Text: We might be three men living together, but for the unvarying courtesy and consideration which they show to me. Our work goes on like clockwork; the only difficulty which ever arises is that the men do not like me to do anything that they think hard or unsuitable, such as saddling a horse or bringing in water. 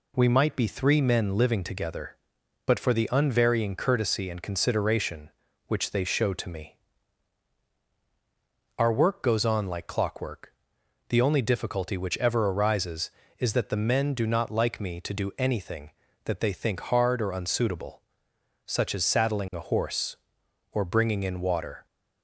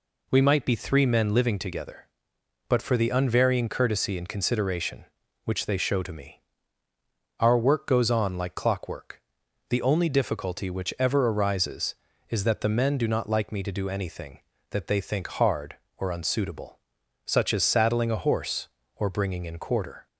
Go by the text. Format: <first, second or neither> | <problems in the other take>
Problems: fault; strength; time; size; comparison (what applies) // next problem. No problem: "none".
first | says "quarter" for "water"; at 19.5 s